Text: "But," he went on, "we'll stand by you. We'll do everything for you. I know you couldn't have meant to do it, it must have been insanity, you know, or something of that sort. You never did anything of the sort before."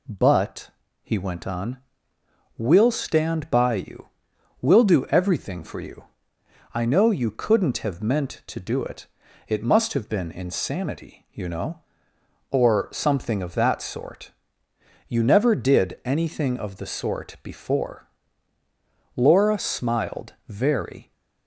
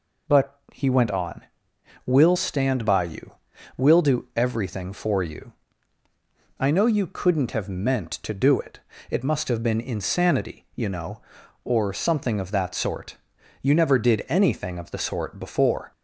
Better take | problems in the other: second | goes on to say "Laura smiled very"; strong; from 19.1 s on; 1.9 s long

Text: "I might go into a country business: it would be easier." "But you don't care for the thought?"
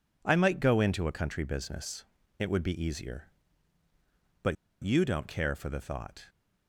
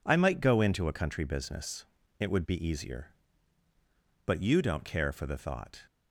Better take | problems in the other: second | pauses between "But" and "you"; slight; at 4.5 s; 0.28 s long

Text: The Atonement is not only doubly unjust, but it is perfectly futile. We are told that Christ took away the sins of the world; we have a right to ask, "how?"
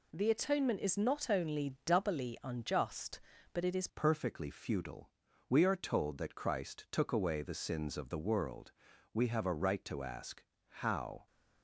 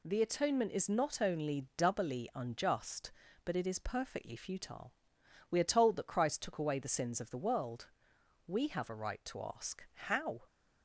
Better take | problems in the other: second | changes voice at "perfectly"; from 3.8 s on; 7.4 s long

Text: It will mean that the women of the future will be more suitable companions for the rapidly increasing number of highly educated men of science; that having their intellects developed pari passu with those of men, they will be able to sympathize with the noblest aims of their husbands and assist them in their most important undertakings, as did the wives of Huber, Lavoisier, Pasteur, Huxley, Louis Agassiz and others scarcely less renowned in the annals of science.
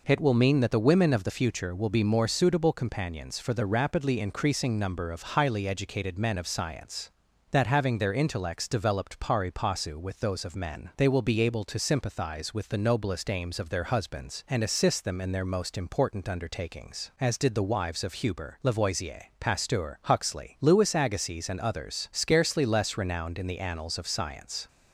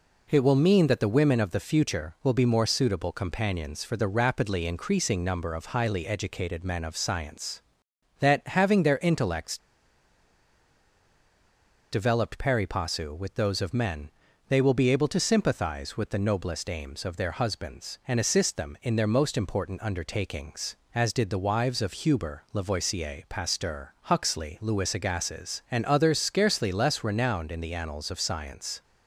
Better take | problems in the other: first | pauses between "intellects" and "developed"; strong; at 9.5 s; 2.3 s long

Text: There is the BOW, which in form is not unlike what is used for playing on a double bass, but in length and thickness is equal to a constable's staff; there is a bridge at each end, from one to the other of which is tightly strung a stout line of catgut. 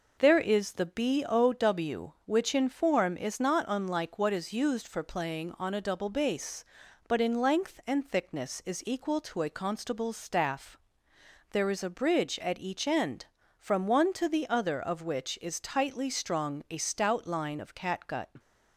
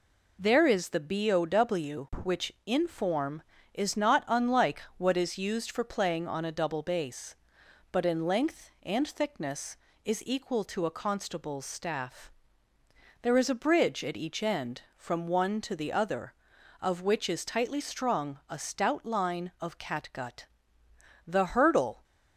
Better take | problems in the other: first | goes on to say "The HURDLE"; noticeable; from 21.2 s on; 0.78 s long

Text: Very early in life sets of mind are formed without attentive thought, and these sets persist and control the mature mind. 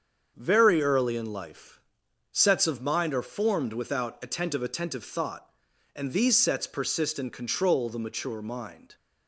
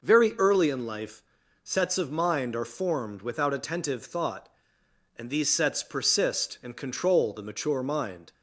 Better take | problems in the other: second | starts louder than the rest; until 1.3 s; 7 dB // pauses between "life" and "sets"; noticeable; at 1.7 s; 0.54 s long; also in the second // says "attentive" twice; at 4.6 s

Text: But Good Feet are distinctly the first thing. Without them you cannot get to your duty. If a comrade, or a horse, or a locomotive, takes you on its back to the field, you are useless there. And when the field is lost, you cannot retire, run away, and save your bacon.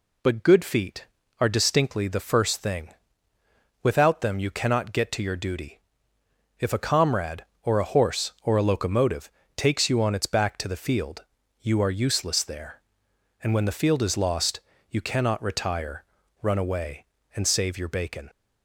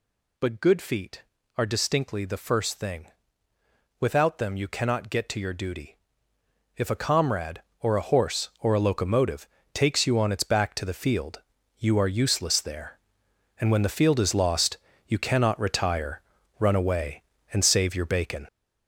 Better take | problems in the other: first | gets louder; throughout; 6.5 dB

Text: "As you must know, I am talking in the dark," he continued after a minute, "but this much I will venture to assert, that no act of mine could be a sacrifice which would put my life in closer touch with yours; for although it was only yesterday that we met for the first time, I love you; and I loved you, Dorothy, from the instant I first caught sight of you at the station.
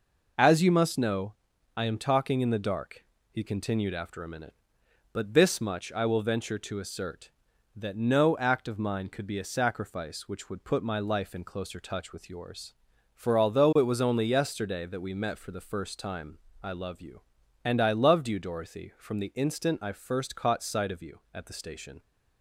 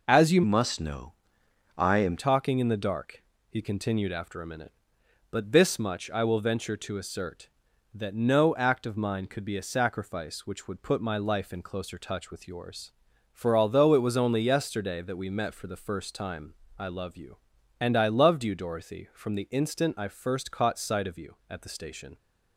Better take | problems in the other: first | changes voice from "must" to "am"; from 0.4 to 2.1 s; 1.7 s long

